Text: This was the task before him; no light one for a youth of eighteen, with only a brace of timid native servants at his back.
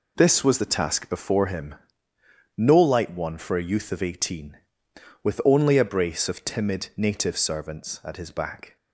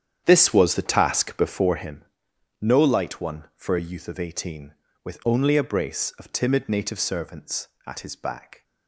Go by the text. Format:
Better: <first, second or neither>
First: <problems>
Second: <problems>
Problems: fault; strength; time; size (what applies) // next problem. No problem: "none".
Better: first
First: none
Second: starts louder than the rest; strong; until 2.1 s; 9 dB